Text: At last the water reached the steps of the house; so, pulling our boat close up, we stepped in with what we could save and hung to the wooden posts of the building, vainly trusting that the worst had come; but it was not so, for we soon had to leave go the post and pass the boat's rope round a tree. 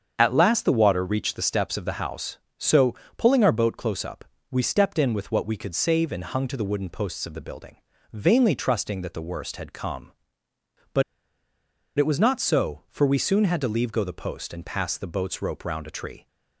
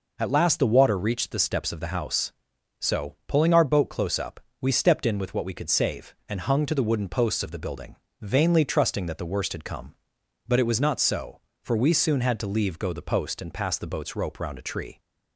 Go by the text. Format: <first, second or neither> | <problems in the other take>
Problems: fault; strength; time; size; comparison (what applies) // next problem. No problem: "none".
second | starts louder than the rest; strong; until 1.1 s; 7.5 dB // pauses between "but" and "it"; noticeable; at 11.0 s; 0.93 s long